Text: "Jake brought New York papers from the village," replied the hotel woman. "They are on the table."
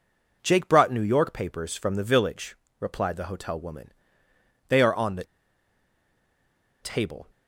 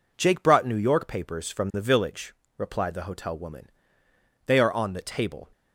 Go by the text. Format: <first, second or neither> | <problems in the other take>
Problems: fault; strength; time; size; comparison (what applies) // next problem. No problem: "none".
second | pauses between "the" and "table"; strong; at 5.2 s; 1.5 s long